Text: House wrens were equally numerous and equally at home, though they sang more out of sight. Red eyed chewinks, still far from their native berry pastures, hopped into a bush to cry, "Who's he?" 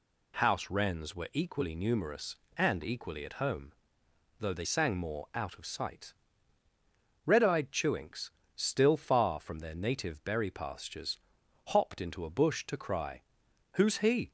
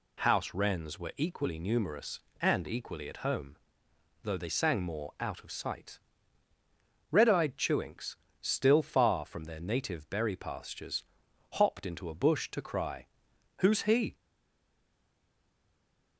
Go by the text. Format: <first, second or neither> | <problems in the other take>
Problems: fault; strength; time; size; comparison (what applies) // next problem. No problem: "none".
first | stays silent after the last word; noticeable; from 14.1 s on; 2.0 s long